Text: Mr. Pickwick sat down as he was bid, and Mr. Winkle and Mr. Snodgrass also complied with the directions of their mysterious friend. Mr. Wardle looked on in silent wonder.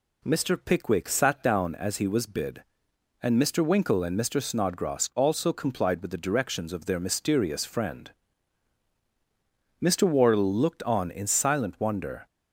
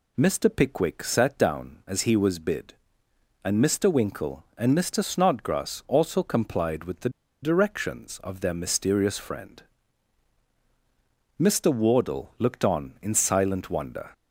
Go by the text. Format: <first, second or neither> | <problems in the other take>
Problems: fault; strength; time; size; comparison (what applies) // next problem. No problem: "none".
first | pauses between "the" and "directions"; slight; at 7.0 s; 0.33 s long